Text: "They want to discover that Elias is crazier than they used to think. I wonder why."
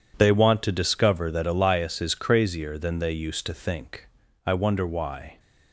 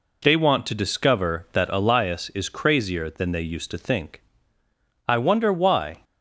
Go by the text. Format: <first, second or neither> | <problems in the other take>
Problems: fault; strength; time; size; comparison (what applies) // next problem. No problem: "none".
neither | none